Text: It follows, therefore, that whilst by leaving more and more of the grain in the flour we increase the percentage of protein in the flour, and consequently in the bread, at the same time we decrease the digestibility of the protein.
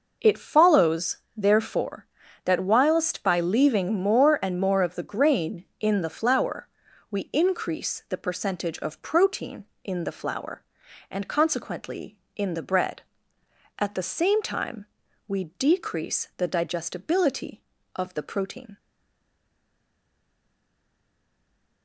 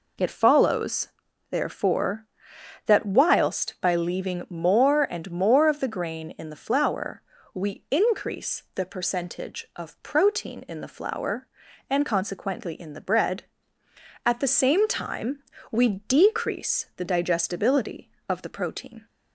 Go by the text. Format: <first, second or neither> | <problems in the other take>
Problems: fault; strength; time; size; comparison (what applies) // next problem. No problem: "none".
second | pauses between "flour" and "we"; at 6.6 s; 0.42 s long; slight in the second // pauses between "time" and "we"; at 14.8 s; 0.42 s long; slight in the second // stays silent after the last word; strong; from 18.7 s on; 3.1 s long